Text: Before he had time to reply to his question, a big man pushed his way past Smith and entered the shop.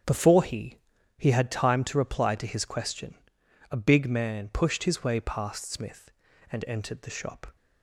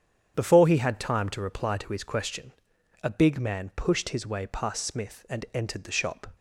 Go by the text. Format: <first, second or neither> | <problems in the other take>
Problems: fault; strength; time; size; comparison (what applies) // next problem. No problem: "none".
second | starts louder than the rest; strong; until 1.4 s; 8.5 dB; strong in the second // says "he" twice; at 1.1 s